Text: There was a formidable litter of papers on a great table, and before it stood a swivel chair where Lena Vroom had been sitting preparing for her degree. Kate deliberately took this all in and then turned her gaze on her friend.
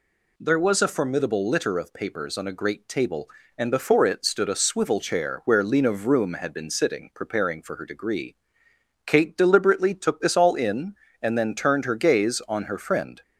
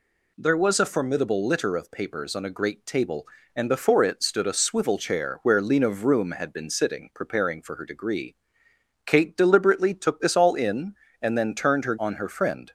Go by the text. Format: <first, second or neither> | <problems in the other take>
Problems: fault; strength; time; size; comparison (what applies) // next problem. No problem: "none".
first | skips "gaze"; at 11.9 s